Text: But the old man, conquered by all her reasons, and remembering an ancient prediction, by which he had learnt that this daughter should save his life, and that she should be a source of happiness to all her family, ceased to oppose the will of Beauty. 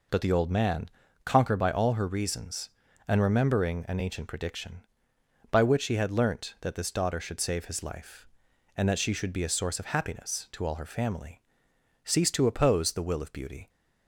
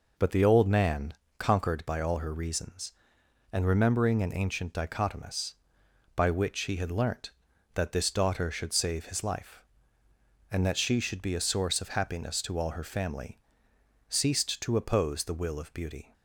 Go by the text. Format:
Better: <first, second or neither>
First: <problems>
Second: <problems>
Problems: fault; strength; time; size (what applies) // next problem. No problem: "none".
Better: first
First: none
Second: says "dichotomous" for "prediction"; at 4.7 s